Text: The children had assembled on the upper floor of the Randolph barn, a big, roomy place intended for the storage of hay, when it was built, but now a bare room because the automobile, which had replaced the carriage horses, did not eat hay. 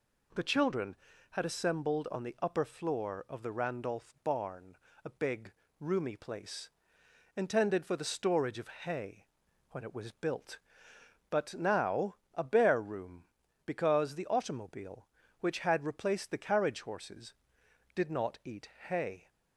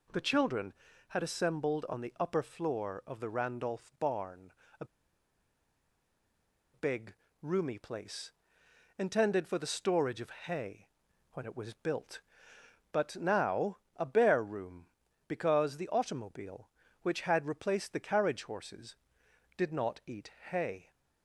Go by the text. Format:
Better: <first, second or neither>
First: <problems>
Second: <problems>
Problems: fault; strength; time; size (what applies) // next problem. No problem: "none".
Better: first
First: pauses between "place" and "intended"; noticeable; at 6.7 s; 0.66 s long // pauses between "now" and "a"; slight; at 12.1 s; 0.18 s long // pauses between "eat" and "hay"; slight; at 18.6 s; 0.20 s long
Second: pauses between "a" and "big"; strong; at 4.8 s; 1.8 s long // pauses between "place" and "intended"; noticeable; at 8.3 s; 0.66 s long // pauses between "now" and "a"; slight; at 13.7 s; 0.18 s long // pauses between "eat" and "hay"; slight; at 20.3 s; 0.20 s long